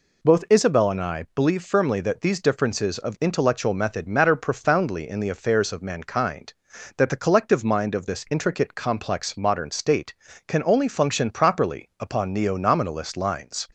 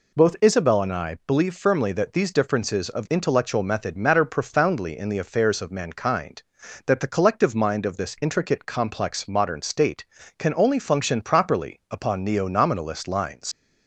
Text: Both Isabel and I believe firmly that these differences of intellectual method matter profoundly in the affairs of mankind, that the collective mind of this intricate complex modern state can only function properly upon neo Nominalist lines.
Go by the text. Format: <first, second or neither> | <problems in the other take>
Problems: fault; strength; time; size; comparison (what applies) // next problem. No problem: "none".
first | leaves "lines" unfinished; at 13.5 s; 95 ms